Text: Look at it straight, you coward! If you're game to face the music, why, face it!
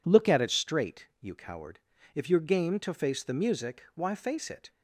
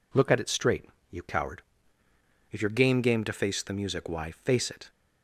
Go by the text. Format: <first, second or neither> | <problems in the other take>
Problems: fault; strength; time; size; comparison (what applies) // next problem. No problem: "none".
first | says "game" twice; at 3.0 s